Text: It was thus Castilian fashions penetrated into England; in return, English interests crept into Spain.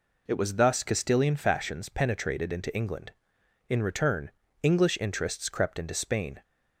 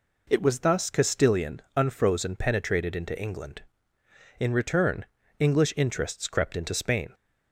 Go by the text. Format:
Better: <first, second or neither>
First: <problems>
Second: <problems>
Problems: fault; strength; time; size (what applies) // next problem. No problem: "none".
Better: first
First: none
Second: says "unfrozen" for "fashions"; at 1.7 s